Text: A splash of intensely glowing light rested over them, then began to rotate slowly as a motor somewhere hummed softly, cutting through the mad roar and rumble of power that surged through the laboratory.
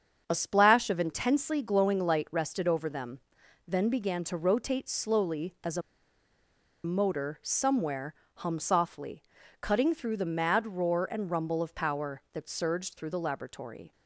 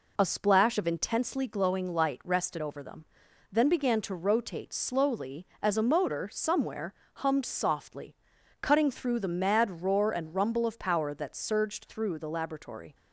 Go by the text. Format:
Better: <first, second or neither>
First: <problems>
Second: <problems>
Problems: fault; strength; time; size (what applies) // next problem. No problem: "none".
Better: second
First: starts louder than the rest; strong; until 1.2 s; 7 dB // pauses between "a" and "motor"; at 5.8 s; 1.0 s long // pauses between "somewhere" and "hummed"; slight; at 8.1 s; 0.22 s long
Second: pauses between "somewhere" and "hummed"; slight; at 6.9 s; 0.22 s long